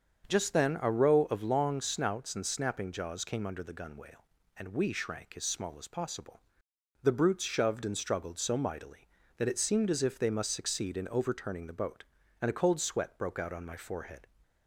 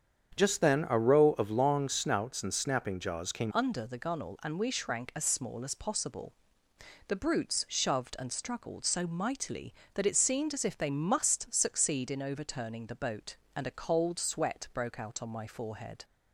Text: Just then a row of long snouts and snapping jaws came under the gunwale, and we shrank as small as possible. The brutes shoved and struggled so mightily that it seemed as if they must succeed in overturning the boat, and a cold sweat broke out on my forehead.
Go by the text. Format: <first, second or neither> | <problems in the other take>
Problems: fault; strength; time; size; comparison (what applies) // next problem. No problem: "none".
first | starts louder than the rest; strong; until 1.3 s; 7.5 dB; also in the first // changes voice at "under"; from 3.5 s on; 12.5 s long